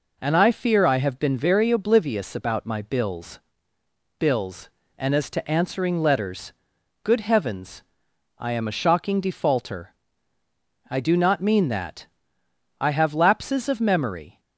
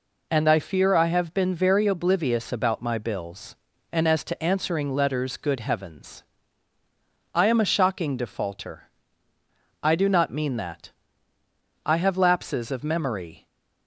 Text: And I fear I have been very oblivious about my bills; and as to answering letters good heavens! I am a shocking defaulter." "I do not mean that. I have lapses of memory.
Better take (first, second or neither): second